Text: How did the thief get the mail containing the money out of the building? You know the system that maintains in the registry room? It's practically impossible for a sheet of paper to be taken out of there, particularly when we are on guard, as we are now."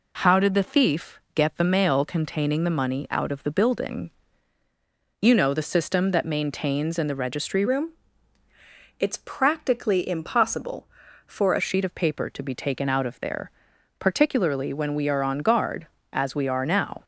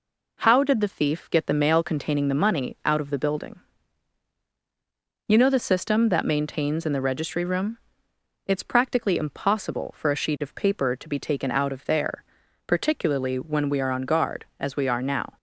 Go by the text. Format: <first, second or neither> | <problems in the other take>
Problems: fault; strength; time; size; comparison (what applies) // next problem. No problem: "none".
second | changes voice from "room" to "a"; from 7.6 to 11.6 s; 4.0 s long